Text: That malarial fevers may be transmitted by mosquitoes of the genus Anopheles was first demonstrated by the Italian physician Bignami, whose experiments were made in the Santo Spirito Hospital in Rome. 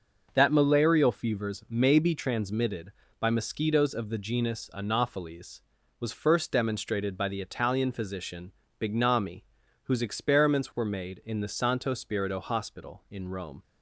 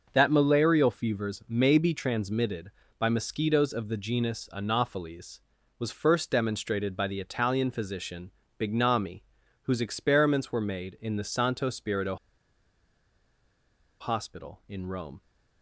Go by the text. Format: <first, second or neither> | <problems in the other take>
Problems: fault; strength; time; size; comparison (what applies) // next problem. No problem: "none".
first | pauses between "physician" and "Bignami"; slight; at 8.3 s; 0.28 s long; slight in the first // pauses between "Spirito" and "Hospital"; strong; at 12.1 s; 1.8 s long